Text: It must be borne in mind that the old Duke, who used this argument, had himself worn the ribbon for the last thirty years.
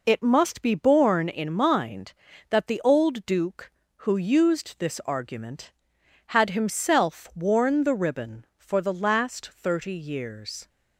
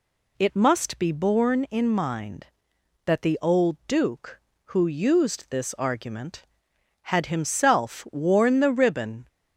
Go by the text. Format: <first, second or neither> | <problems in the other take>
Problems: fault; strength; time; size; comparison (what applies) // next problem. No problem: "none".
first | stops before "for the last thirty years"; at 9.2 s